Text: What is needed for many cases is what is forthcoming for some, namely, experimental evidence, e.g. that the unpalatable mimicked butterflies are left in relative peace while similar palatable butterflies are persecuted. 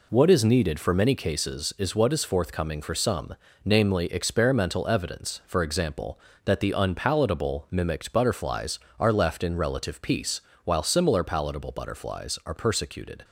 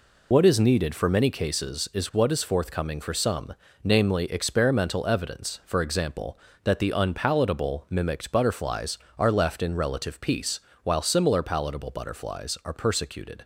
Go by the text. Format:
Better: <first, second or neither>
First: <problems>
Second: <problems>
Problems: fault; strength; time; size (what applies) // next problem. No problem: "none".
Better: first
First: pauses between "peace" and "while"; slight; at 10.4 s; 0.24 s long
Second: loses the start of "What"; at 0.3 s; 50 ms // pauses between "peace" and "while"; slight; at 10.5 s; 0.24 s long